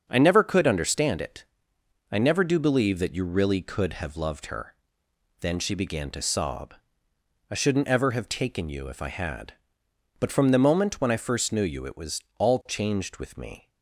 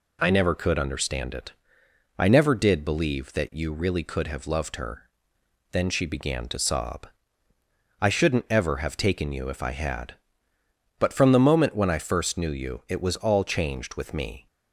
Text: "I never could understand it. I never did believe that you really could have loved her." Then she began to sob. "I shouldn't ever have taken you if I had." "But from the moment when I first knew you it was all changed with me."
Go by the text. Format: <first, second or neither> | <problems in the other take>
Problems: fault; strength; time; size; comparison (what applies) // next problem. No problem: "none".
second | starts louder than the rest; until 1.1 s; 7 dB // says "do" for "did"; at 2.4 s // pauses between "was" and "all"; slight; at 12.2 s; 0.16 s long